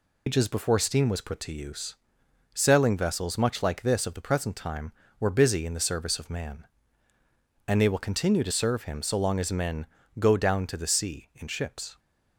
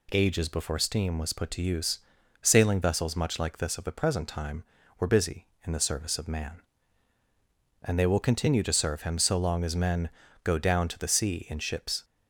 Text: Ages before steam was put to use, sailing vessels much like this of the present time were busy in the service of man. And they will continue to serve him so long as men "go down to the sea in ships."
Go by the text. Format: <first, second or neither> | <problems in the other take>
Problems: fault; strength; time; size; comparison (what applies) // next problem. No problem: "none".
second | loses the start of "Ages"; at 0.2 s; 130 ms // pauses between "men" and "go"; slight; at 9.8 s; 0.32 s long; slight in the second